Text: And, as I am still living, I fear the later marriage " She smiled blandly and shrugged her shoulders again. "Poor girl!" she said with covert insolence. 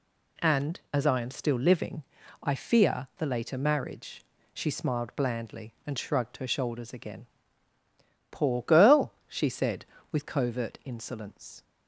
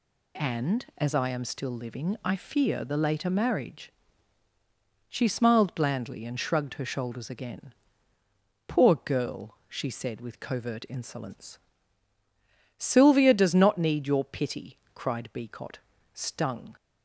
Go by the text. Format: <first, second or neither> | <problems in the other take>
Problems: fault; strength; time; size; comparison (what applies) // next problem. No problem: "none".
first | goes on to say "Sylvia does not need your pity cried Beecot stung"; strong; from 12.7 s on; 3.9 s long